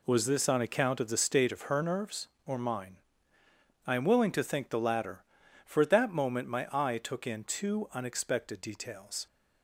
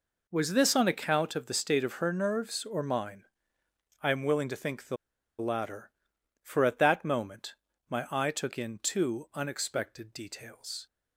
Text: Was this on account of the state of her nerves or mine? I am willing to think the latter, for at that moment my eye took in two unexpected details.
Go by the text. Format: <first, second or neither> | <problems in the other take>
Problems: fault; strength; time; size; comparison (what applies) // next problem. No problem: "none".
first | pauses between "the" and "latter"; at 4.9 s; 0.43 s long // pauses between "moment" and "my"; slight; at 7.5 s; 0.34 s long